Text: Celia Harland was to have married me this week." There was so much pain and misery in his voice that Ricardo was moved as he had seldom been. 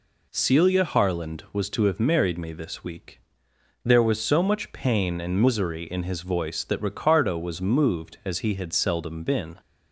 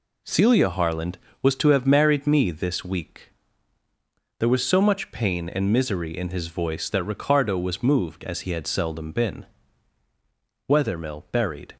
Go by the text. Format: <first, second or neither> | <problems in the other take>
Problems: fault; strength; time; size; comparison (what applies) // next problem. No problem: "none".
first | goes on to say "Wethermill buried"; noticeable; from 10.6 s on; 1.0 s long